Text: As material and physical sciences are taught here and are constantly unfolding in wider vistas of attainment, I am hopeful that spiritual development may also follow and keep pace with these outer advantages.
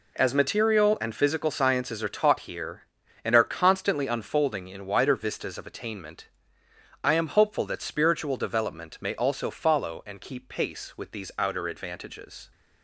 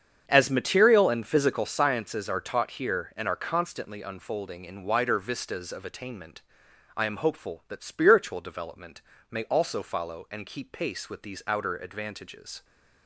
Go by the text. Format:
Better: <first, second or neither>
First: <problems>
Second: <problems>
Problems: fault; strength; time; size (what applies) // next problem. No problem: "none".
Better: first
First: none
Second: starts louder than the rest; strong; until 1.7 s; 7.5 dB // pauses between "development" and "may"; slight; at 9.0 s; 0.28 s long